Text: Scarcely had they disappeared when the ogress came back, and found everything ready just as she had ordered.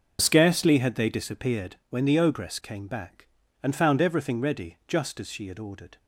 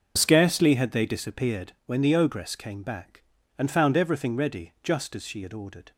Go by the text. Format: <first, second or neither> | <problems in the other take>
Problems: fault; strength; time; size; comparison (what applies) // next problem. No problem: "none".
neither | starts louder than the rest; noticeable; the same in both